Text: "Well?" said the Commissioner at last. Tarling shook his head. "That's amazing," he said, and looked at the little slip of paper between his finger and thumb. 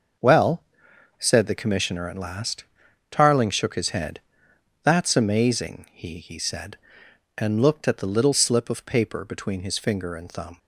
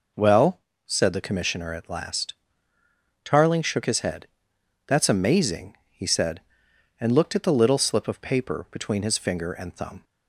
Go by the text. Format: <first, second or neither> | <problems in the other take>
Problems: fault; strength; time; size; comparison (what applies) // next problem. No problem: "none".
second | starts louder than the rest; until 1.7 s; 6 dB // says "he" twice; at 6.1 s